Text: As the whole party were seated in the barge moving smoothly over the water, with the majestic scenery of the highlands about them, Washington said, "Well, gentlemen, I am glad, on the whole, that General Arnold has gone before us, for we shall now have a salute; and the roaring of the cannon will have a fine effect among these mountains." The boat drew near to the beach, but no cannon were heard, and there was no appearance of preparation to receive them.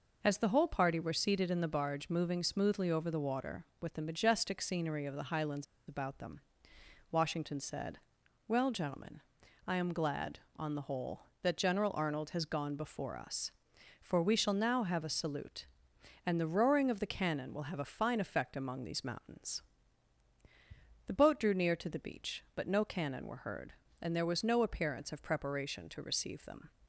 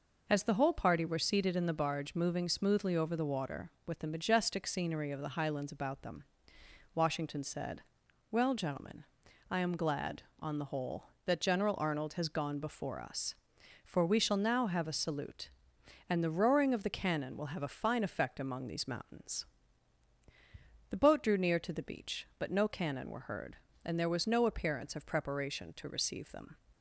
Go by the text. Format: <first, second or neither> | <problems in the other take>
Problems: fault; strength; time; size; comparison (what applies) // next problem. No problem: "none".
second | pauses between "highlands" and "about"; slight; at 5.6 s; 0.22 s long